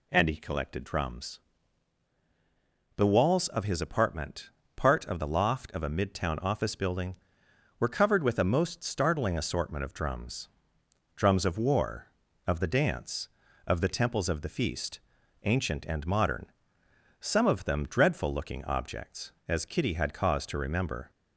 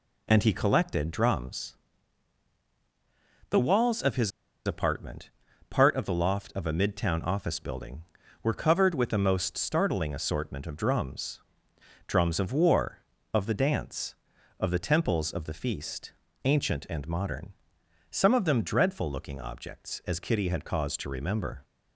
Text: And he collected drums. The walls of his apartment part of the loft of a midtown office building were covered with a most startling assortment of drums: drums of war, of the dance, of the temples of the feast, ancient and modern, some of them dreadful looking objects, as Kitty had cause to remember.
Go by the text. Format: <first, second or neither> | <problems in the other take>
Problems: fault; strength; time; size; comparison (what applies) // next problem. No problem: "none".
first | pauses between "his" and "apartment"; slight; at 4.3 s; 0.35 s long // pauses between "apartment" and "part"; at 5.2 s; 0.38 s long; slight in the first